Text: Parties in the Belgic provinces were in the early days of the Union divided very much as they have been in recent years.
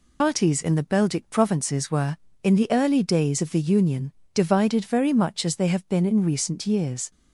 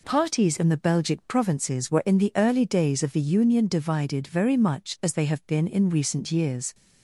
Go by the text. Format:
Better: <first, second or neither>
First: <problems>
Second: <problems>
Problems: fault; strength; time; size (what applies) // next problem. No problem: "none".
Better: second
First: loses the start of "Parties"; at 0.2 s; 125 ms // pauses between "Union" and "divided"; slight; at 4.1 s; 0.22 s long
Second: none